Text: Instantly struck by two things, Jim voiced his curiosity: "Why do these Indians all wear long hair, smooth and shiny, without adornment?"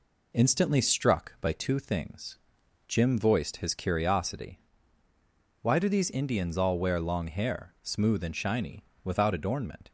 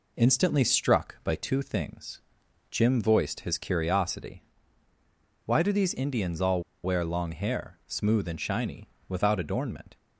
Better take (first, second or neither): first